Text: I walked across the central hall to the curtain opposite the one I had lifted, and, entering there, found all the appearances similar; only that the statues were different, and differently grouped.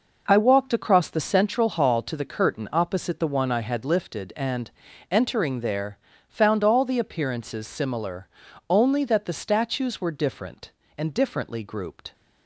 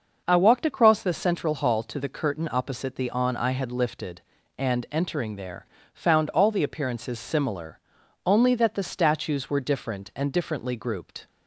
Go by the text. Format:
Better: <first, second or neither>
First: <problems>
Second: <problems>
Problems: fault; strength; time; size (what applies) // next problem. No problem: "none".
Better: first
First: none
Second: starts louder than the rest; noticeable; until 1.2 s; 6 dB // says "on" for "one"; at 3.1 s